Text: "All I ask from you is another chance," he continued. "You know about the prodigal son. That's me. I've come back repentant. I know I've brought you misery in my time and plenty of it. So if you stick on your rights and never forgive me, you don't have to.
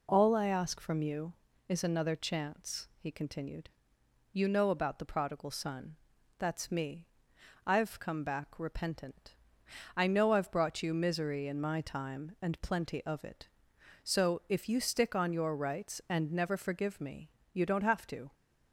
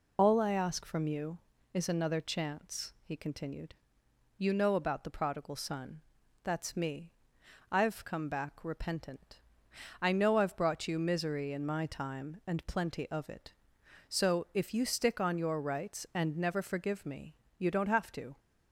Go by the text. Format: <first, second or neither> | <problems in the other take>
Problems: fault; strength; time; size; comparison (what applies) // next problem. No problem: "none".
first | loses the start of "All"; at 0.1 s; 55 ms